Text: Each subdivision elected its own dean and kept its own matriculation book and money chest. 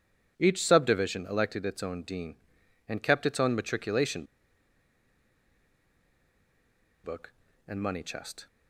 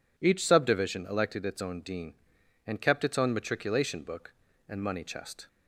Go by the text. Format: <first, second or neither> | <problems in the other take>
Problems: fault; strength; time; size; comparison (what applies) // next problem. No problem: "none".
second | pauses between "matriculation" and "book"; strong; at 4.2 s; 2.7 s long